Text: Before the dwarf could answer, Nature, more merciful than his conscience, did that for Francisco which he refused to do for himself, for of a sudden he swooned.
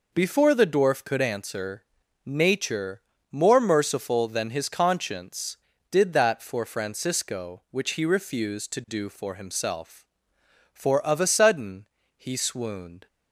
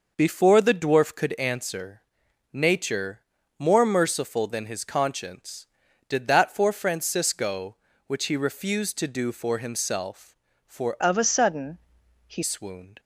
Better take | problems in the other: first | changes voice from "of" to "he"; from 11.0 to 12.4 s; 1.4 s long // pauses between "sudden" and "he"; noticeable; at 11.7 s; 0.50 s long; slight in the first

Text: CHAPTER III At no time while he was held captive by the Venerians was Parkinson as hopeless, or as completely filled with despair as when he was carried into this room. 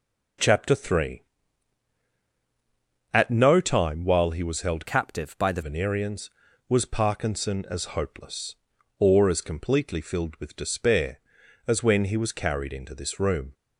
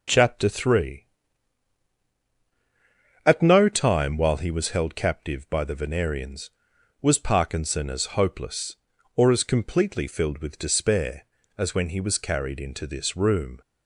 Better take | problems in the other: second | changes voice from "captive" to "the"; from 4.8 to 5.6 s; 0.8 s long

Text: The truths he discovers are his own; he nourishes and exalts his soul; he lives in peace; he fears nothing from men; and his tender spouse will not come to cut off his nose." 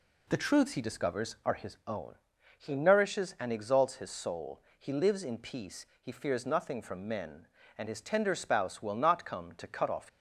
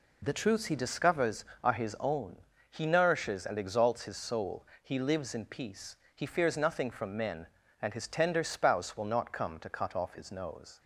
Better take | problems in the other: second | stops before "his nose"; at 10.0 s

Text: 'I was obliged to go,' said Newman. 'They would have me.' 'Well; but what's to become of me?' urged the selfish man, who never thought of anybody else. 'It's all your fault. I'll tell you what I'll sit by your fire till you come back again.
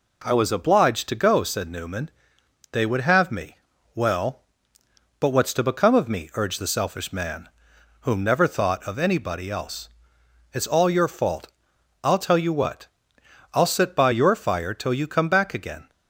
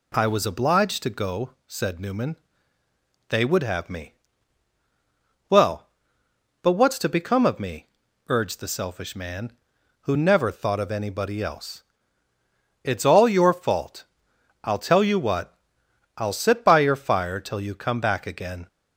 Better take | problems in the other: second | says "whom" for "who"; at 8.0 s // pauses between "what" and "I'll"; noticeable; at 12.8 s; 0.68 s long; noticeable in the second

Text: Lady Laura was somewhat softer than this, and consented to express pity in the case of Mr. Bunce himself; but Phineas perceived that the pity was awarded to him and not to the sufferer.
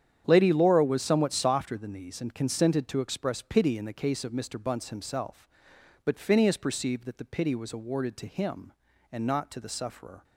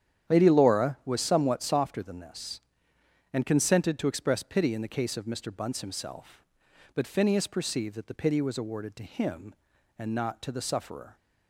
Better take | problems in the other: second | starts louder than the rest; strong; until 1.2 s; 9 dB; strong in the second // says "these" for "this"; at 1.9 s

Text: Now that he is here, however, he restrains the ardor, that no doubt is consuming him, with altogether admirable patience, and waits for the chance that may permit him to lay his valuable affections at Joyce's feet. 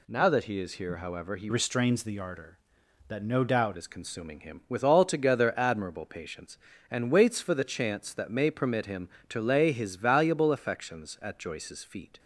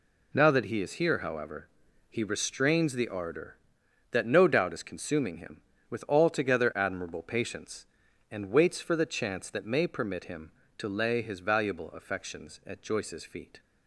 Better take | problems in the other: second | changes voice from "restrains" to "doubt"; from 1.4 to 3.7 s; 2.3 s long

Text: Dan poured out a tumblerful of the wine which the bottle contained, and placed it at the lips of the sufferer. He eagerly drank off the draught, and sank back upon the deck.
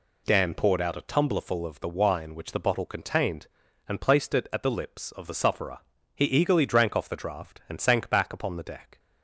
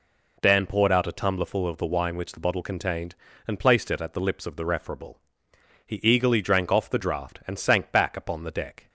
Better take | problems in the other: first | says "referable" for "sufferer"; at 4.6 s

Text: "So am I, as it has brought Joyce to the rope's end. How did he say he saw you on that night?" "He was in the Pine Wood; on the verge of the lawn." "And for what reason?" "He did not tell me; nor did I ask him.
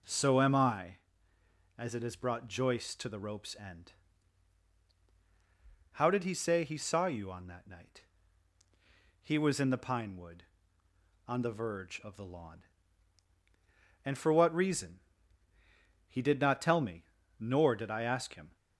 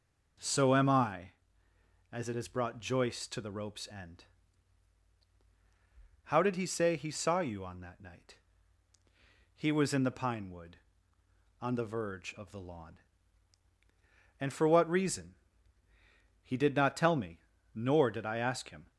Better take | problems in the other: neither | none

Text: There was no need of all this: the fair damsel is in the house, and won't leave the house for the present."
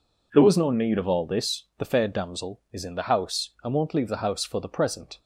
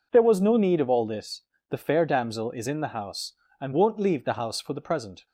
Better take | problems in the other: neither | none

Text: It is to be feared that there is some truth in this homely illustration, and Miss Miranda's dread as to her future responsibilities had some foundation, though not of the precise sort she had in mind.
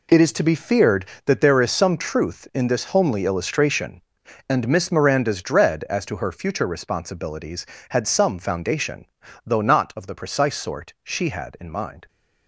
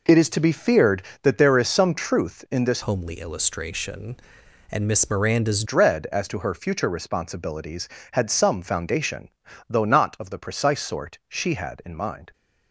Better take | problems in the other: first | changes voice from "homely" to "Miranda's"; from 2.8 to 5.6 s; 2.8 s long

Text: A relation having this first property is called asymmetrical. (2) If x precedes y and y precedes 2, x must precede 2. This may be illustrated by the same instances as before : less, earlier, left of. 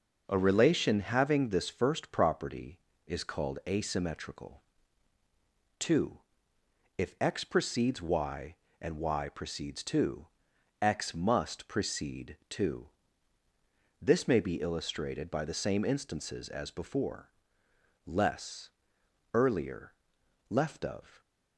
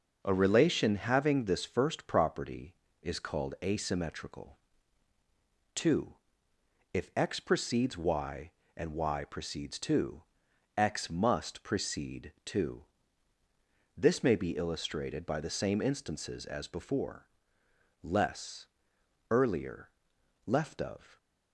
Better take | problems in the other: neither | none

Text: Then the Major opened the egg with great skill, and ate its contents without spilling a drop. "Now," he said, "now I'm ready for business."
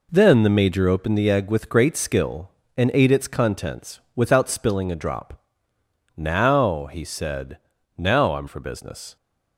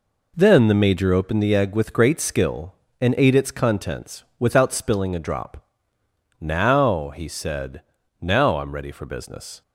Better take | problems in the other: second | pauses between "contents" and "without"; slight; at 3.9 s; 0.16 s long; slight in the second // skips "ready"; at 8.4 s

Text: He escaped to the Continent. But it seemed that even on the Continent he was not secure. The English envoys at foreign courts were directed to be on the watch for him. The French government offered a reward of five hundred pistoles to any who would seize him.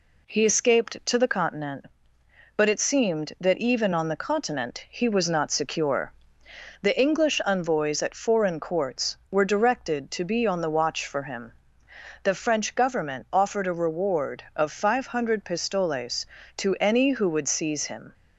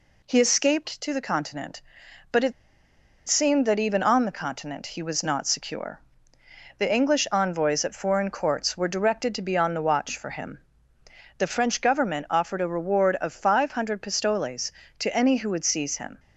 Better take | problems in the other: first | pauses between "it" and "seemed"; noticeable; at 2.5 s; 0.74 s long

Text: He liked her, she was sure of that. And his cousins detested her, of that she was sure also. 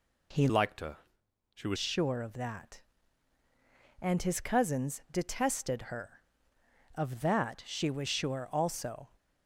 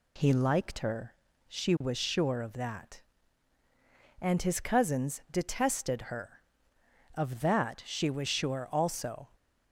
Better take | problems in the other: second | changes voice from "liked" to "was"; from 0.4 to 1.7 s; 1.3 s long

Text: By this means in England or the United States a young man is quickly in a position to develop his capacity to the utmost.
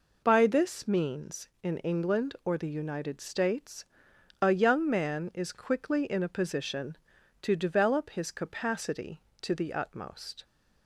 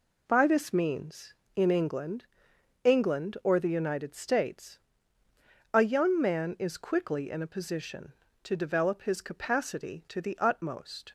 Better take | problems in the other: first | says "England" twice; at 2.8 s // pauses between "States" and "a"; noticeable; at 4.7 s; 0.94 s long; noticeable in the first

